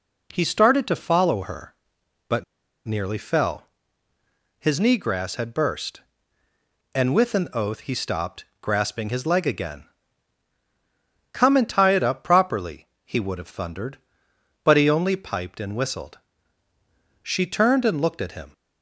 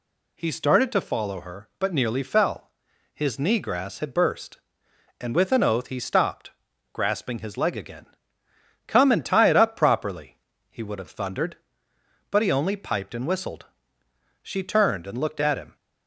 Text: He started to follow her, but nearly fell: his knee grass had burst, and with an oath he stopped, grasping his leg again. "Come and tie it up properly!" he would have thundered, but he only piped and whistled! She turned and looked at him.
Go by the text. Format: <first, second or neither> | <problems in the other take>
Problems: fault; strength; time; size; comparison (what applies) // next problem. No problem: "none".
second | pauses between "but" and "nearly"; at 2.4 s; 0.42 s long